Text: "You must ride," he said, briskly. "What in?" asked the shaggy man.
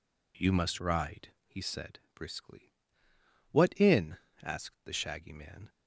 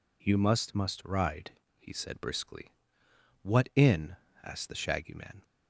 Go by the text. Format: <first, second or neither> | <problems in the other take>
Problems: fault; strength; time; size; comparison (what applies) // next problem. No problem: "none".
first | says "must" twice; at 0.7 s